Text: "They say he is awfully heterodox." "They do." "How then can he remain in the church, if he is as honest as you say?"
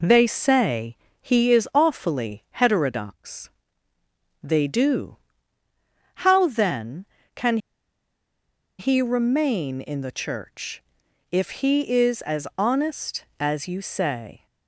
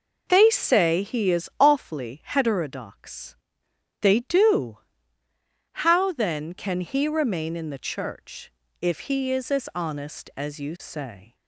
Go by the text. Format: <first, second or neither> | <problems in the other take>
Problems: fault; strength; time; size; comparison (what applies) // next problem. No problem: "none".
second | pauses between "say" and "he"; slight; at 0.9 s; 0.26 s long // pauses between "can" and "he"; at 7.5 s; 1.2 s long